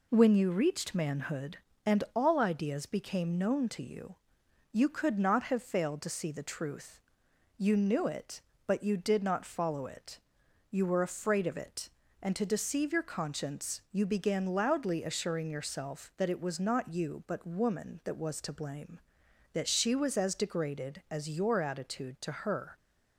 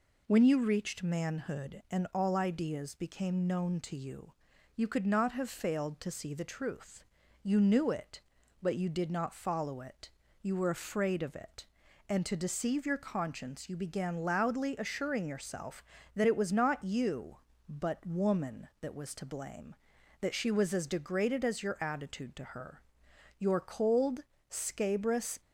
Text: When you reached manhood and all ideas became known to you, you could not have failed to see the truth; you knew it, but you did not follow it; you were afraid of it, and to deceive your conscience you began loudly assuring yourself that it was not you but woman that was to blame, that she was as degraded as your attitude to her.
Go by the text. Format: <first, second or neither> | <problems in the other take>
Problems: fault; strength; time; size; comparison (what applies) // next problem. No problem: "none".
first | goes on to say "Your cold scabrous"; strong; from 23.3 s on; 2.0 s long